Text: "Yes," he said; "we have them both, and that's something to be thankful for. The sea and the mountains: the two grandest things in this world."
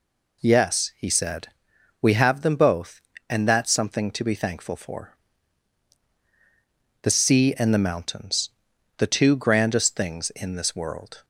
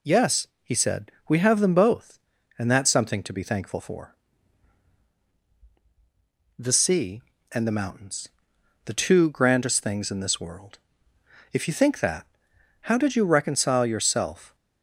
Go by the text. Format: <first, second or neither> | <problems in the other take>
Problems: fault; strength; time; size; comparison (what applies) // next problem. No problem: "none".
first | goes on to say "If you think that how did you reconcile yourself"; strong; from 11.5 s on; 3.0 s long